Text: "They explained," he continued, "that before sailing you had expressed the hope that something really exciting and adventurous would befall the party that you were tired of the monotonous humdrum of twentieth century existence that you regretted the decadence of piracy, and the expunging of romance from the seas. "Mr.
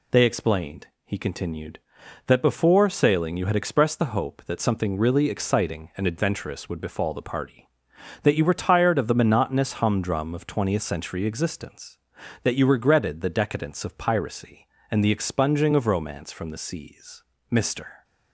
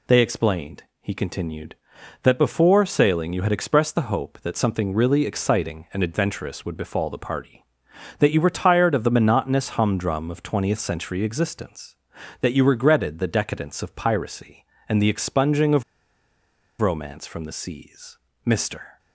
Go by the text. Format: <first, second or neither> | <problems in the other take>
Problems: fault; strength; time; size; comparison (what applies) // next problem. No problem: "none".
first | pauses between "of" and "romance"; noticeable; at 15.8 s; 0.97 s long